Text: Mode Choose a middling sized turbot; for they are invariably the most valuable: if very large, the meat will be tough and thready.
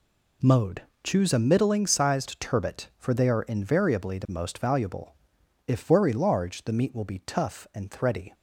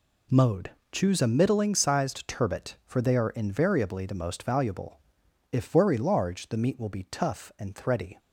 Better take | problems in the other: neither | pauses between "Mode" and "Choose"; slight; the same in both

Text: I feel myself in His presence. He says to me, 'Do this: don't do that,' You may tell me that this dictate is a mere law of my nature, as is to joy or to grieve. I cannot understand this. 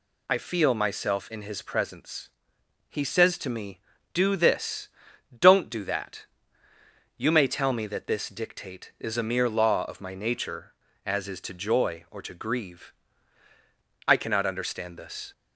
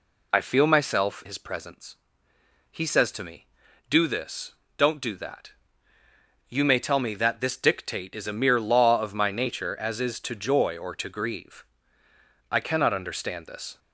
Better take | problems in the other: first | skips "in"; at 1.2 s

